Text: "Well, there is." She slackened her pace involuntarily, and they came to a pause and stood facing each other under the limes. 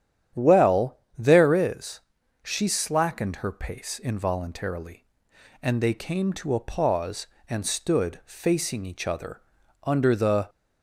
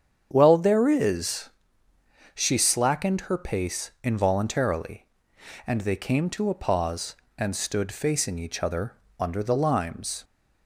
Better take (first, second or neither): second